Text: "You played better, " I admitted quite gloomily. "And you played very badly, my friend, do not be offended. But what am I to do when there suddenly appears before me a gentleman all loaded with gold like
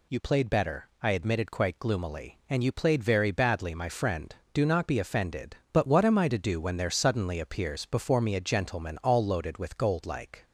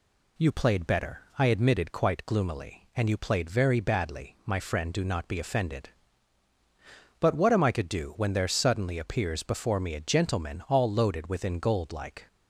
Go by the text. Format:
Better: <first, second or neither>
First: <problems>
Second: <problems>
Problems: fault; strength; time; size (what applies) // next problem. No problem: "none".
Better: first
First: none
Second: says "within" for "with"; at 11.2 s